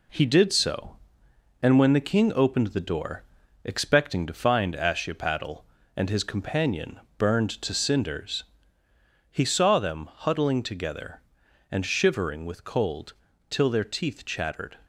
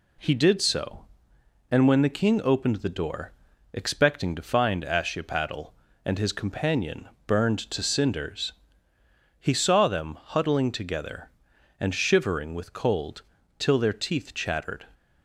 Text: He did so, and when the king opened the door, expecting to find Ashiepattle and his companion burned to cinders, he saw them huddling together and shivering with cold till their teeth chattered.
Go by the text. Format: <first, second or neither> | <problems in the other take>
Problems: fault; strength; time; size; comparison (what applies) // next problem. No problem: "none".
second | gets quieter; noticeable; throughout; 4.5 dB // pauses between "companion" and "burned"; slight; at 6.9 s; 0.18 s long; slight in the second // pauses between "cold" and "till"; at 13.1 s; 0.38 s long; also in the second